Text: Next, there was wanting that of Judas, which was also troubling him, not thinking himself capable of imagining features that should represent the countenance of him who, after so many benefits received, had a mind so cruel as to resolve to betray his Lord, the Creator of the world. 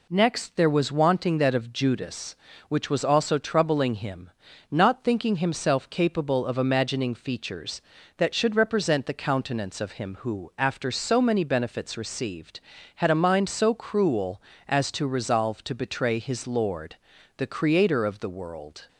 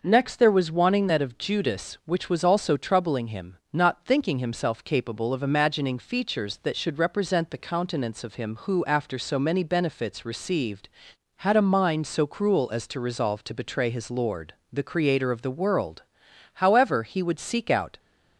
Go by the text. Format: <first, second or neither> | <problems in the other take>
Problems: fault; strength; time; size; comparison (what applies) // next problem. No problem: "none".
first | goes on to say "However he would seek out"; from 16.5 s on; 1.4 s long